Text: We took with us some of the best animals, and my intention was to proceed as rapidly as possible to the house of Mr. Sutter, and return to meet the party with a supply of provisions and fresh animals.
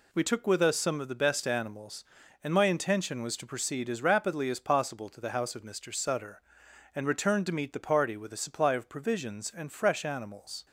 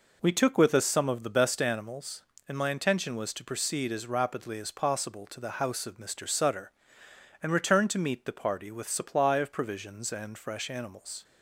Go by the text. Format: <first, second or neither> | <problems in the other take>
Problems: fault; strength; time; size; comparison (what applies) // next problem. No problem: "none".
first | skips "a"; at 8.8 s